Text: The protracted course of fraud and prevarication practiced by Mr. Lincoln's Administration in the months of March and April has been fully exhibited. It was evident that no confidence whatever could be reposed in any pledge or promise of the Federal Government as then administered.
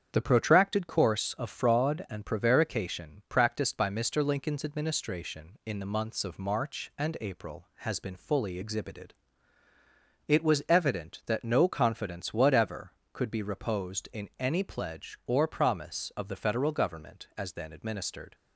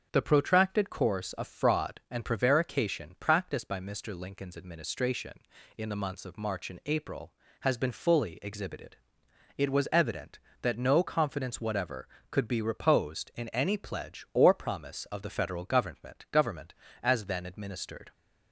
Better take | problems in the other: first | starts louder than the rest; until 1.1 s; 6.5 dB; strong in the first // says "Government" twice; at 16.3 s

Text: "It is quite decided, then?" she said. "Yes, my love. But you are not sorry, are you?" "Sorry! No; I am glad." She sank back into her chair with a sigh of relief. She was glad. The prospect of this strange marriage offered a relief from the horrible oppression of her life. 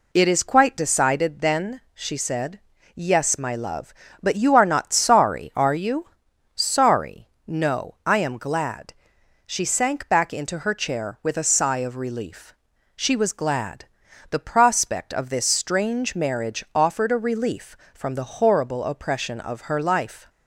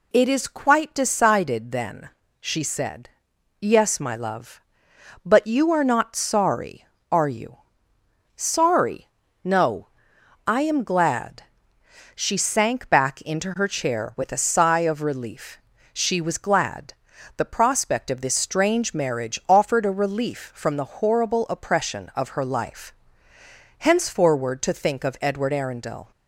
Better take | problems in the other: first | goes on to say "Henceforward to think of Edward Arundel"; strong; from 23.7 s on; 2.3 s long

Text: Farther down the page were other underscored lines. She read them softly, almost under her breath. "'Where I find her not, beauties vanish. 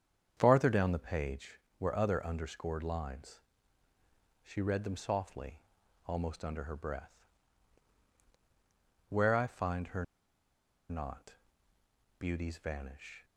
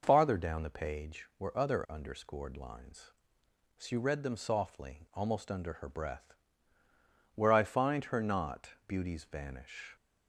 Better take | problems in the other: second | starts louder than the rest; strong; until 1.3 s; 8 dB // pauses between "her" and "not"; noticeable; at 10.0 s; 0.85 s long

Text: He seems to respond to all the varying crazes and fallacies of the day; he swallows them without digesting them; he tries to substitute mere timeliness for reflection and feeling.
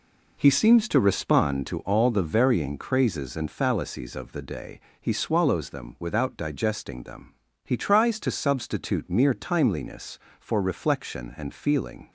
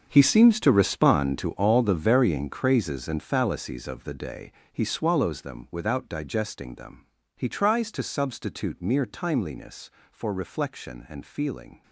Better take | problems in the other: first | gets quieter; strong; throughout; 14.5 dB

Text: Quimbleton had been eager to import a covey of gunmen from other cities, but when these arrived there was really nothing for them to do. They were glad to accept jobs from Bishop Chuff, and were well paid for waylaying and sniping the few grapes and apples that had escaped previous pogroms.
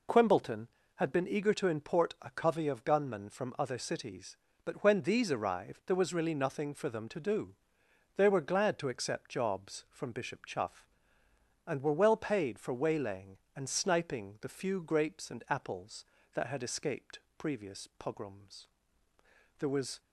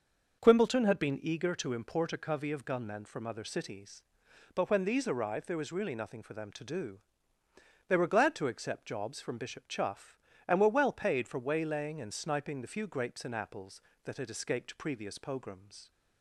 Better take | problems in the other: second | pauses between "escaped" and "previous"; slight; at 17.1 s; 0.18 s long // goes on to say "There was"; slight; from 19.5 s on; 0.40 s long

